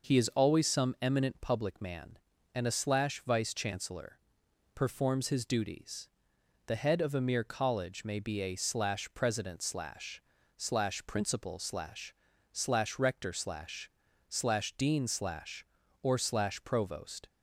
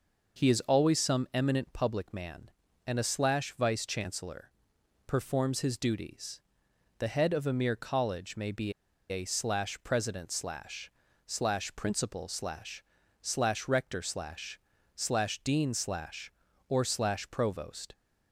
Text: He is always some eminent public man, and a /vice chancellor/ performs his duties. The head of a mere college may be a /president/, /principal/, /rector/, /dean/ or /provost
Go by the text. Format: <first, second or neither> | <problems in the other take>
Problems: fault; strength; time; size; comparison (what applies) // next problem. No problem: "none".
first | pauses between "be" and "a"; at 8.7 s; 0.37 s long